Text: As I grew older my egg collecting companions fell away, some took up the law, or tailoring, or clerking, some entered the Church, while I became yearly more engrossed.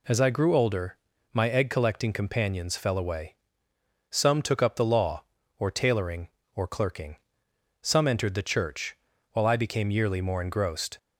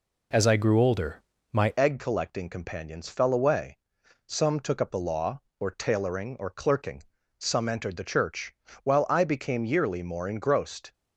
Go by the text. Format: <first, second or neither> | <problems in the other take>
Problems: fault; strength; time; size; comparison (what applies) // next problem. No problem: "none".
first | pauses between "older" and "my"; slight; at 1.1 s; 0.32 s long; slight in the first // changes voice at "egg"; from 1.7 s on; 9.2 s long